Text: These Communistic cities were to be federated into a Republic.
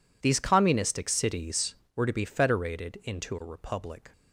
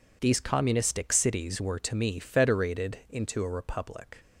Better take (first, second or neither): first